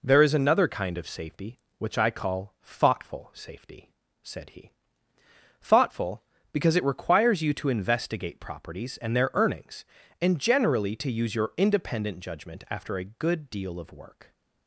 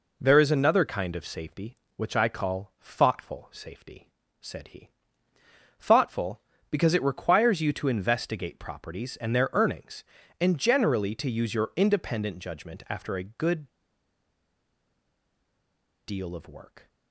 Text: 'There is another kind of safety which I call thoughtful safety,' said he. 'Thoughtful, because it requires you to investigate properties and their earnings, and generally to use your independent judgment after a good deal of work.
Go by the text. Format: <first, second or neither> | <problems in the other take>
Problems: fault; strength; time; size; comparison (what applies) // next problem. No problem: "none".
first | pauses between "good" and "deal"; strong; at 13.6 s; 2.3 s long